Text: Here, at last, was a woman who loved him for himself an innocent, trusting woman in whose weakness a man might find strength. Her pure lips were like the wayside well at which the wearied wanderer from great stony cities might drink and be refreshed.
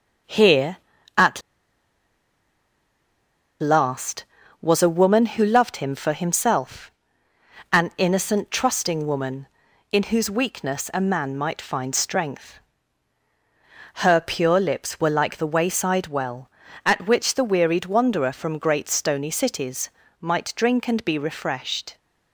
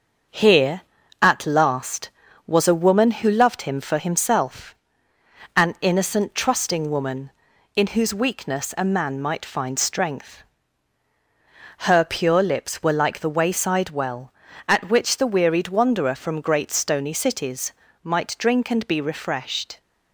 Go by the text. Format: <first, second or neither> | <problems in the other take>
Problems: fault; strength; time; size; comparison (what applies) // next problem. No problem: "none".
second | starts louder than the rest; until 3.8 s; 6.5 dB; also in the second // pauses between "at" and "last"; strong; at 1.4 s; 2.2 s long // pauses between "himself" and "an"; noticeable; at 6.8 s; 0.82 s long; noticeable in the second // pauses between "cities" and "might"; slight; at 19.8 s; 0.32 s long; slight in the second